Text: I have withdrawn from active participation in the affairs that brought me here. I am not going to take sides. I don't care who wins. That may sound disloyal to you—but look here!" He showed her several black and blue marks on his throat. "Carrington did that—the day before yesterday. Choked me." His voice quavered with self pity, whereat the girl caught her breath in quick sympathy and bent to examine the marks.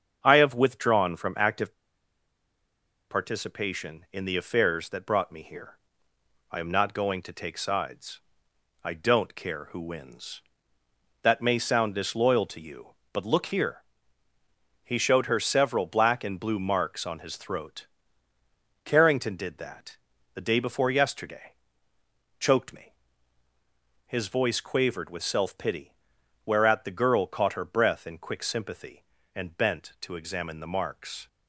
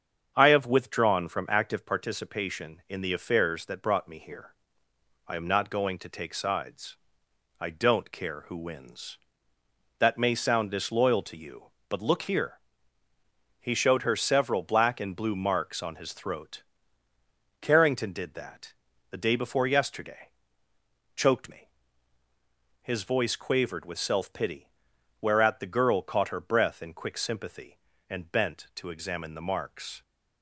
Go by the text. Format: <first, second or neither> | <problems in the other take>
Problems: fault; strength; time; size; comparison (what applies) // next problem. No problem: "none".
second | starts louder than the rest; strong; until 1.2 s; 7.5 dB; strong in the second // pauses between "active" and "participation"; strong; at 1.7 s; 1.3 s long